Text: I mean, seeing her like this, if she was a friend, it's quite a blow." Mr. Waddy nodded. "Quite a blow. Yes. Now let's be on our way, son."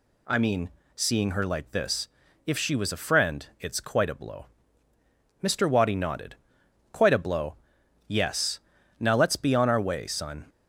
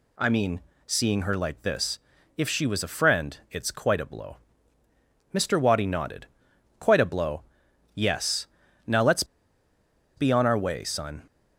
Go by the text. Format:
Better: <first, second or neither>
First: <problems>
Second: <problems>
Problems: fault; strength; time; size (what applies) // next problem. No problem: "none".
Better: first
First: none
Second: pauses between "let's" and "be"; noticeable; at 9.2 s; 0.92 s long